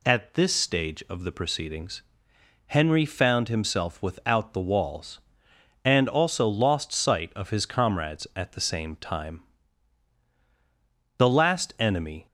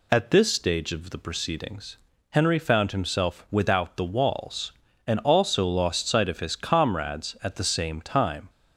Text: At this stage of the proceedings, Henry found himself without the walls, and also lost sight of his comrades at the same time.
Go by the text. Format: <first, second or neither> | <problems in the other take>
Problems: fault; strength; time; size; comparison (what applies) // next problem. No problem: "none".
second | goes on to say "The last enemy"; noticeable; from 11.1 s on; 1.0 s long